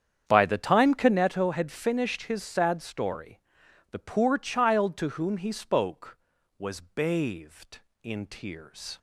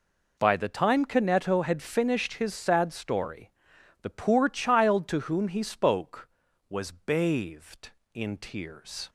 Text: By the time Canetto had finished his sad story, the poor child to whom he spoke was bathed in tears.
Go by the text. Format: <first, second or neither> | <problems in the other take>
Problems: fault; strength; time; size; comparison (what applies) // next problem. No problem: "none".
second | starts louder than the rest; strong; until 1.3 s; 8.5 dB